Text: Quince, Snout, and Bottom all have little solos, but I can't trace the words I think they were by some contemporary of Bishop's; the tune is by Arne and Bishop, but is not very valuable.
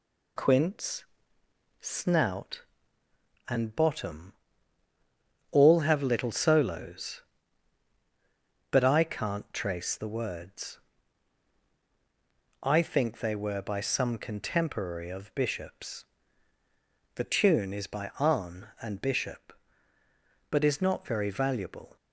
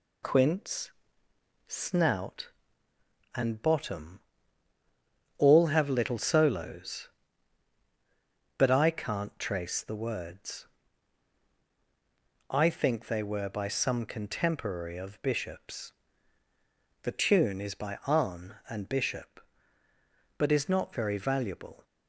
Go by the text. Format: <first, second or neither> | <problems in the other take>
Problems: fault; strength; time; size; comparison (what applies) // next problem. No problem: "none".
neither | pauses between "Bottom" and "all"; the same in both // pauses between "words" and "I"; strong; the same in both